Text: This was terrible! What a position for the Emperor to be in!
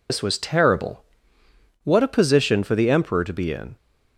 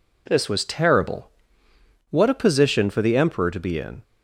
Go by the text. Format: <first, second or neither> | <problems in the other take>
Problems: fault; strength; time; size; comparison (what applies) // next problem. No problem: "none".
second | loses the start of "This"; at 0.0 s; 105 ms